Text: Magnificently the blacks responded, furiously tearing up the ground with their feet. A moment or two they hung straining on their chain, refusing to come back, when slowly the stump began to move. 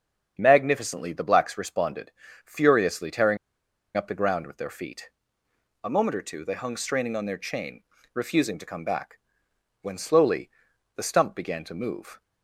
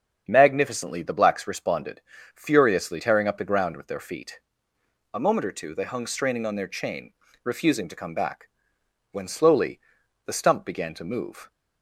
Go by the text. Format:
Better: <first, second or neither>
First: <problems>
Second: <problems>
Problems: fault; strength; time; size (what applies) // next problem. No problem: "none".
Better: second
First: starts louder than the rest; strong; until 1.4 s; 7.5 dB // pauses between "tearing" and "up"; noticeable; at 3.3 s; 0.59 s long // pauses between "slowly" and "the"; noticeable; at 10.4 s; 0.46 s long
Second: starts louder than the rest; strong; until 1.3 s; 7.5 dB // pauses between "slowly" and "the"; noticeable; at 9.7 s; 0.46 s long